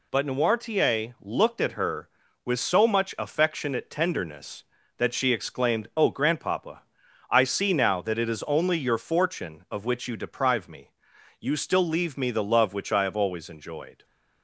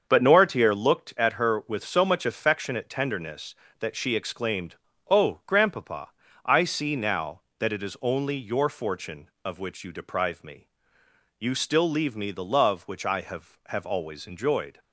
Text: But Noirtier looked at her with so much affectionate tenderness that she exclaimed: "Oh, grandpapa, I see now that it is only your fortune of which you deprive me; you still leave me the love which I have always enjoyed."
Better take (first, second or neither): first